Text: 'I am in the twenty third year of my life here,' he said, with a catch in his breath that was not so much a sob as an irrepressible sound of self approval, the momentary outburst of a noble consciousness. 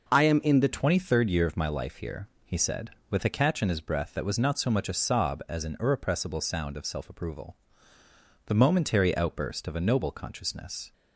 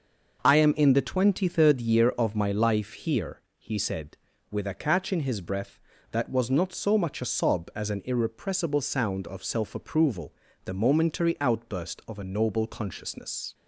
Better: second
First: changes voice at "twenty"; from 0.7 s on; 10.2 s long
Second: none

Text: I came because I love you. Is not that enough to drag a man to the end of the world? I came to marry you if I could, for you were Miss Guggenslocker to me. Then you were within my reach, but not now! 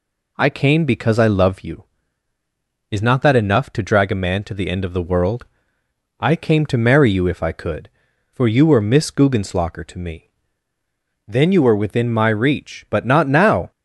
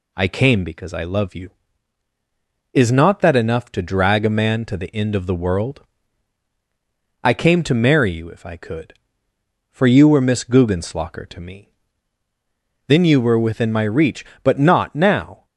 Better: neither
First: none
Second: none

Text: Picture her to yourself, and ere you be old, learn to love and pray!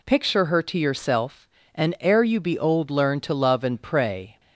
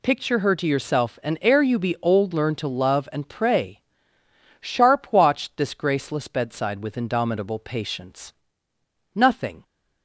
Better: first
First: none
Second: goes on to say "Sharp watched this graceless bedside with indomitable patience Nothing"; strong; from 4.5 s on; 5.0 s long

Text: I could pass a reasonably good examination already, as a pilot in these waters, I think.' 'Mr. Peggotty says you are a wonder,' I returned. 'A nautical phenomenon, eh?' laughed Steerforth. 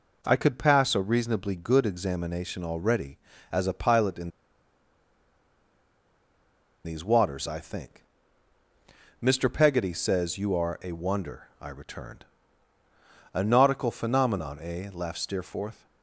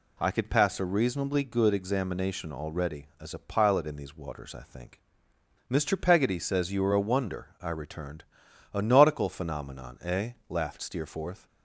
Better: second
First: pauses between "in" and "these"; strong; at 4.2 s; 2.5 s long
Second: none

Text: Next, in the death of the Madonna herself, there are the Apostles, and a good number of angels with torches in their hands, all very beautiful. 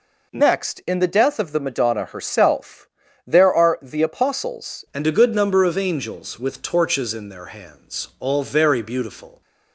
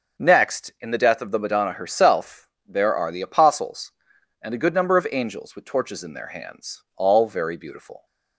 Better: second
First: changes voice at "and"; from 4.9 s on; 4.5 s long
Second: none

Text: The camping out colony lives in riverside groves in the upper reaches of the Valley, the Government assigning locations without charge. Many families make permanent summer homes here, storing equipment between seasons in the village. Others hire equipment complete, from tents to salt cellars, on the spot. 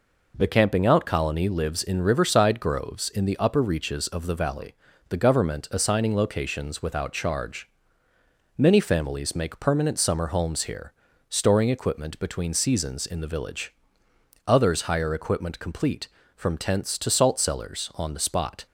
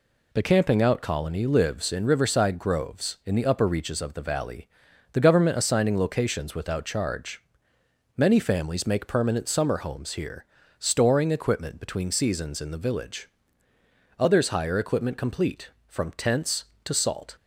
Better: first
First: none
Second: stops before "cellars on the spot"; at 17.3 s

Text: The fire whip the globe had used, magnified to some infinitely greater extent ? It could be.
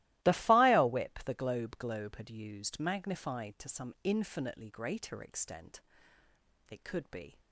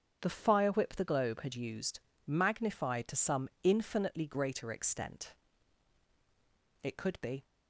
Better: second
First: starts louder than the rest; strong; until 1.2 s; 17 dB // says "globe" twice; at 1.7 s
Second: starts louder than the rest; until 1.2 s; 7 dB

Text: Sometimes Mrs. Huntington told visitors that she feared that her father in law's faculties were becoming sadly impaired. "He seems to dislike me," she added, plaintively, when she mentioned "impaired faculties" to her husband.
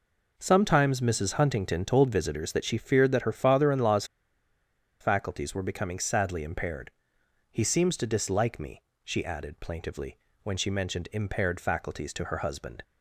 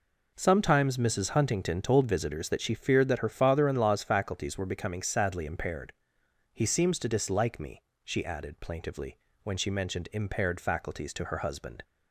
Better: second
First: pauses between "law's" and "faculties"; noticeable; at 4.0 s; 0.96 s long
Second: none

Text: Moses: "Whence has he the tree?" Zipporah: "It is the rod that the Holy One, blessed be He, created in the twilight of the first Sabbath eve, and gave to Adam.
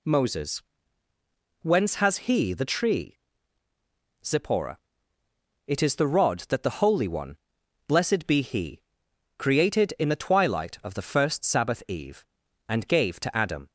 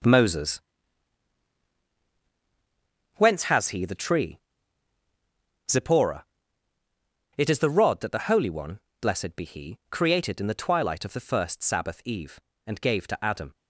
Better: first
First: none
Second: gets quieter; strong; throughout; 11 dB

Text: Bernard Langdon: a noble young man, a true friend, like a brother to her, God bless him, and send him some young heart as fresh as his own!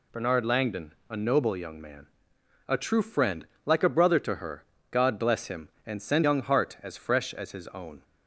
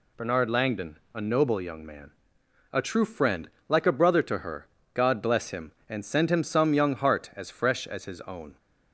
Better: second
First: skips "him some"; at 6.2 s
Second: none

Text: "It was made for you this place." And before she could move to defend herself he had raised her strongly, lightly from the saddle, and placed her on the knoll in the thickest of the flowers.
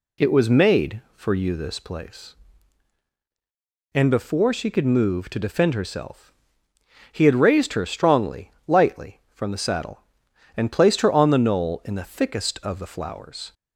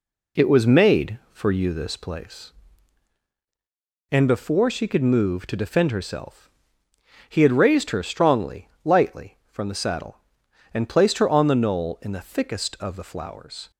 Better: first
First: pauses between "herself" and "he"; noticeable; at 6.3 s; 0.80 s long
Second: gets quieter; noticeable; throughout; 5.5 dB // pauses between "herself" and "he"; noticeable; at 6.5 s; 0.80 s long

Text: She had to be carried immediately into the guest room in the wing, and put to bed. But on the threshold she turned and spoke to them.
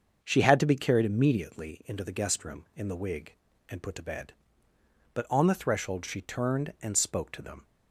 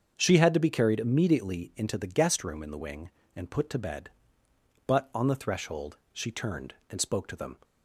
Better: second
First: starts louder than the rest; until 1.2 s; 6.5 dB // says "wig" for "wing"; at 2.9 s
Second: starts louder than the rest; until 1.1 s; 7 dB

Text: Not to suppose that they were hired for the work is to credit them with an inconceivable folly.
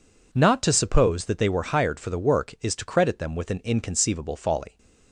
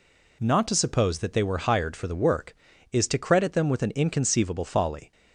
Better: neither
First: none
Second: none

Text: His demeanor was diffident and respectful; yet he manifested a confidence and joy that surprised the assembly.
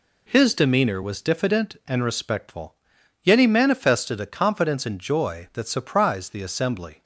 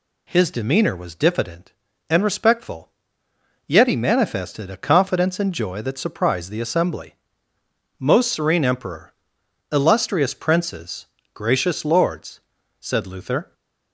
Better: first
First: none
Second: goes on to say "Most serene emperor illustrious princes gracious lords said Luther"; strong; from 7.9 s on; 5.5 s long

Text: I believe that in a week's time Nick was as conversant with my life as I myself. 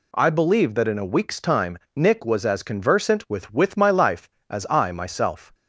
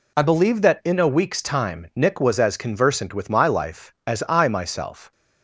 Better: second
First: pauses between "time" and "Nick"; slight; at 1.7 s; 0.16 s long // says "with" twice; at 3.5 s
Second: none

